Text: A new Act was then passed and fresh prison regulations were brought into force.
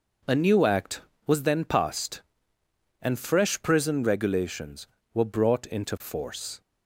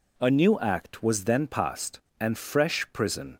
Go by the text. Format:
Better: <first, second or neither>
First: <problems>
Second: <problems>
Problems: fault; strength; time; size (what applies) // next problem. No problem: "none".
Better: first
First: none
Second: stops before "regulations were brought into force"; at 3.3 s